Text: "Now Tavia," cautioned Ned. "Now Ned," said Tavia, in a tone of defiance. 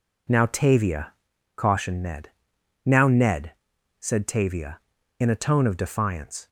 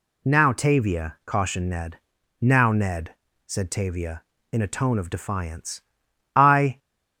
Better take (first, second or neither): first